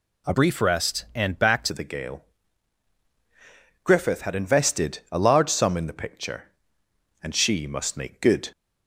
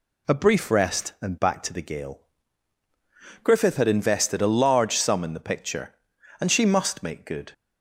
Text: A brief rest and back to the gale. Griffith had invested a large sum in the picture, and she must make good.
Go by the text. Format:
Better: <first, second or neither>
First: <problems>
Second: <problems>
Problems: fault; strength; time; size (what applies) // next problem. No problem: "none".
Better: second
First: changes voice from "brief" to "to"; from 0.3 to 1.7 s; 1.4 s long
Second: none